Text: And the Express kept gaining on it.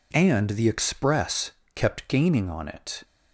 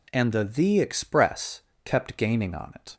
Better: first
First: pauses between "Express" and "kept"; slight; at 1.5 s; 0.22 s long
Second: says "the" twice; at 0.4 s // pauses between "Express" and "kept"; slight; at 1.6 s; 0.24 s long

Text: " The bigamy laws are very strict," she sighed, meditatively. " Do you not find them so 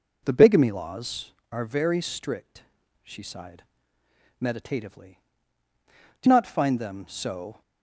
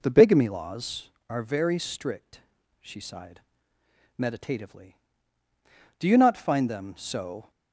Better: second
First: skips "you"; at 6.2 s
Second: none

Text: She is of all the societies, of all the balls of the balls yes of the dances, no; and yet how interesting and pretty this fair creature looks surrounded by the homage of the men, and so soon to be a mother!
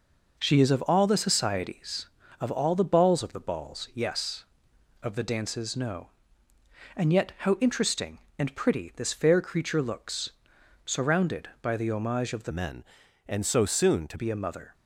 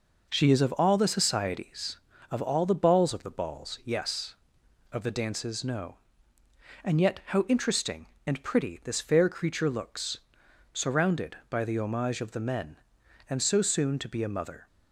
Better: second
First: pauses between "looks" and "surrounded"; noticeable; at 10.3 s; 0.56 s long // changes voice from "men" to "to"; from 12.4 to 14.1 s; 1.7 s long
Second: pauses between "looks" and "surrounded"; noticeable; at 10.1 s; 0.56 s long

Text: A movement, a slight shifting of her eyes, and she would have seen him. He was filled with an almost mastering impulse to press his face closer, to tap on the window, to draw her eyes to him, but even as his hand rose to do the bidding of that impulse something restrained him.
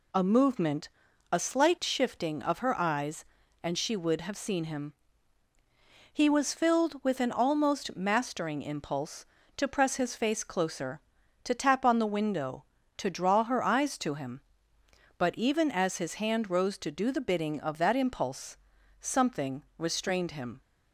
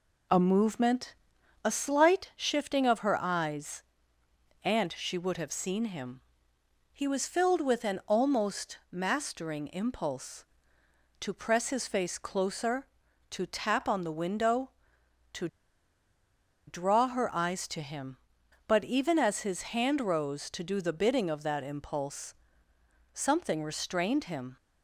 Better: first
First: pauses between "impulse" and "something"; at 18.5 s; 0.44 s long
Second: pauses between "to" and "draw"; at 15.4 s; 1.2 s long // pauses between "impulse" and "something"; noticeable; at 22.3 s; 0.82 s long

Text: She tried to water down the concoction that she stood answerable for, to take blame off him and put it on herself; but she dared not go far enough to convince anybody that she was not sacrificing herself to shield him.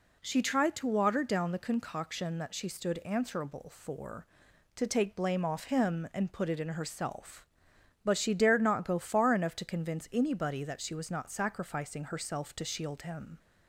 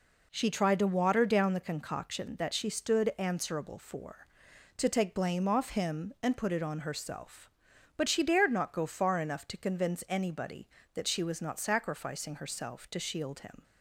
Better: second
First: says "in" for "on"; at 6.6 s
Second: none

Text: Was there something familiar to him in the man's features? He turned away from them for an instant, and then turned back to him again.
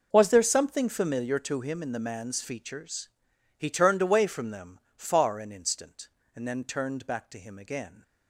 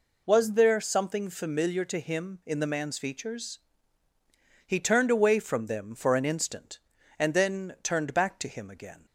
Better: second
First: says "far" for "for"; at 4.9 s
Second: none

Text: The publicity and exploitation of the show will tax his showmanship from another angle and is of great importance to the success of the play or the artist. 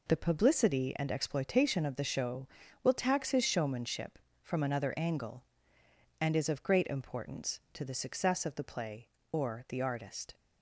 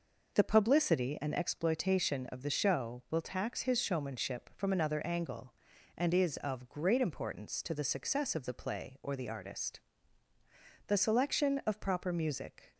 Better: first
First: none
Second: goes on to say "The selection of proper music"; strong; from 10.8 s on; 1.8 s long

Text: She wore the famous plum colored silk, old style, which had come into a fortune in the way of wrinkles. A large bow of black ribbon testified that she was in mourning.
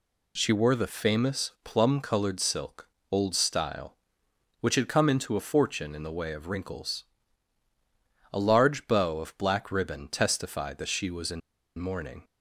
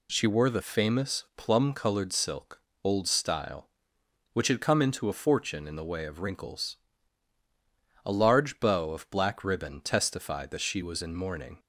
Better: second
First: pauses between "in" and "mourning"; at 11.4 s; 0.37 s long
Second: none

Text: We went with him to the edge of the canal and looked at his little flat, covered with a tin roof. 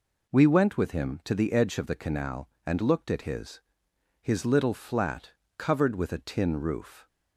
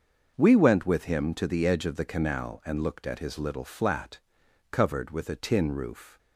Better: second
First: says "his" twice; at 4.1 s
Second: none

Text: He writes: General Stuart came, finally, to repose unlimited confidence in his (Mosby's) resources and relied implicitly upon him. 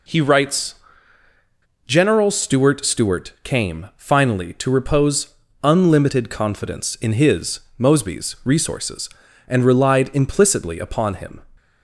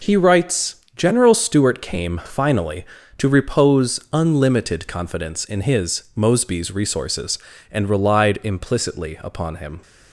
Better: second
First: says "Stuart" twice; at 2.8 s // pauses between "repose" and "unlimited"; slight; at 5.3 s; 0.28 s long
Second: none

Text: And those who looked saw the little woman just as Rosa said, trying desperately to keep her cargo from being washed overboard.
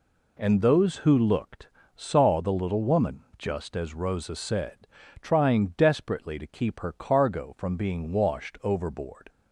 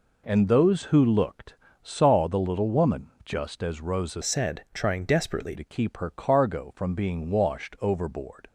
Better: first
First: pauses between "looked" and "saw"; slight; at 1.6 s; 0.28 s long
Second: pauses between "looked" and "saw"; slight; at 1.5 s; 0.28 s long // changes voice from "said" to "desperately"; from 4.2 to 5.5 s; 1.3 s long

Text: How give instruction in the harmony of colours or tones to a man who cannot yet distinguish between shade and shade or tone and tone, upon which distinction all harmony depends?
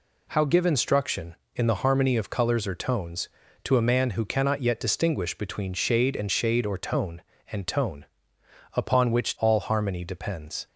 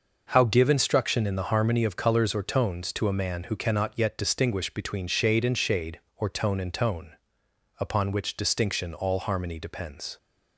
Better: second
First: skips "distinction"; at 9.3 s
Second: none

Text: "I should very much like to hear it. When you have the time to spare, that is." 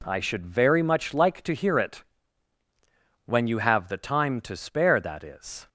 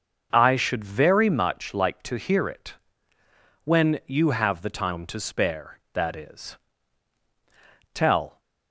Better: first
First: none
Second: starts louder than the rest; until 1.3 s; 6.5 dB // goes on to say "Tell"; slight; from 7.9 s on; 0.46 s long

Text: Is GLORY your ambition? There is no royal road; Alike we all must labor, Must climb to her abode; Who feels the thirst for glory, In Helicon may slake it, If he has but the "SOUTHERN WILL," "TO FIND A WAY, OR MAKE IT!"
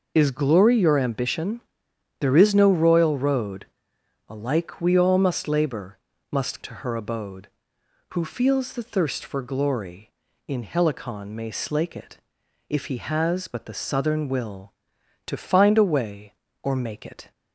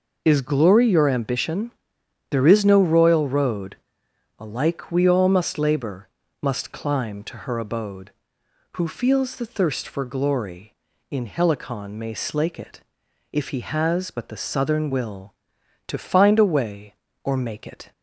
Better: second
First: skips "climb"; at 6.6 s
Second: none

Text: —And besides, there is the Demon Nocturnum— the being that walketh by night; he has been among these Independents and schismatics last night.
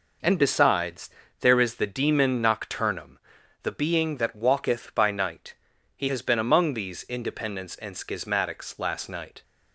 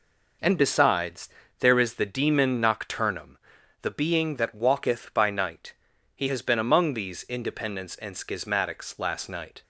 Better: neither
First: none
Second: none

